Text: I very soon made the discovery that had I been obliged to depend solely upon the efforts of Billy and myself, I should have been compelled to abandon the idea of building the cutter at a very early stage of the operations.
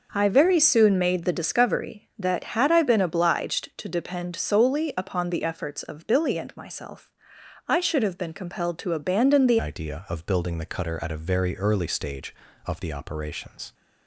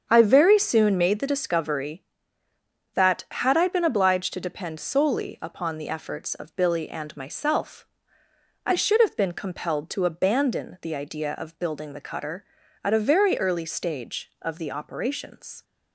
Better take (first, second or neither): second